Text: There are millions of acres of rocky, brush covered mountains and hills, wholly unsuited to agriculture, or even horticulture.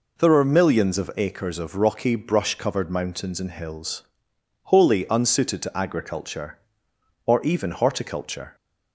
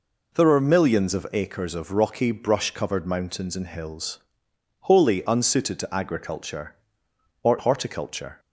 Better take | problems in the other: first | skips "even"; at 7.5 s

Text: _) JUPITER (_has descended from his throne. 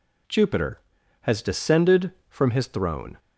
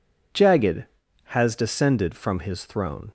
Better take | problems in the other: first | says "Jagged" for "JUPITER"; at 0.3 s

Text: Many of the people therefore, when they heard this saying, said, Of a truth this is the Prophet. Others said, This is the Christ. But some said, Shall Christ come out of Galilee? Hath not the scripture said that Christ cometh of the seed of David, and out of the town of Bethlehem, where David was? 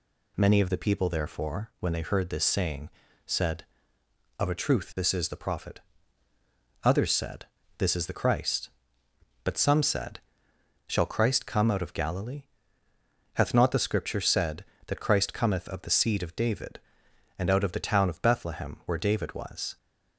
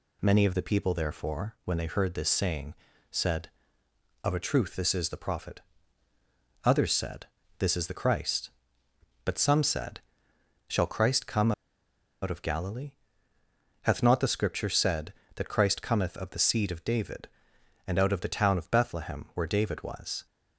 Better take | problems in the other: first | pauses between "come" and "out"; noticeable; at 11.5 s; 0.70 s long

